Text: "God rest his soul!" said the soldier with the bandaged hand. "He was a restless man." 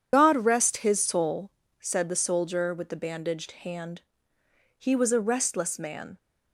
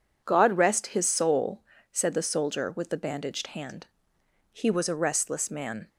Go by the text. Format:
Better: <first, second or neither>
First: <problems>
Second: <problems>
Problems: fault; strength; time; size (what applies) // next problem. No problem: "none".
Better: second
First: loses the start of "God"; at 0.1 s; 40 ms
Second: none